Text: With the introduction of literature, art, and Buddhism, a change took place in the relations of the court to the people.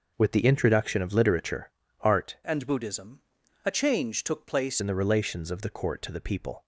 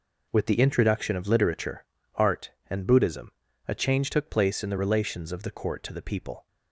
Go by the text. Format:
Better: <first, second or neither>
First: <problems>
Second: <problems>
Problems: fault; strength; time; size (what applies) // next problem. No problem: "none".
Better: second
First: changes voice from "and" to "place"; from 2.4 to 4.8 s; 2.4 s long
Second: none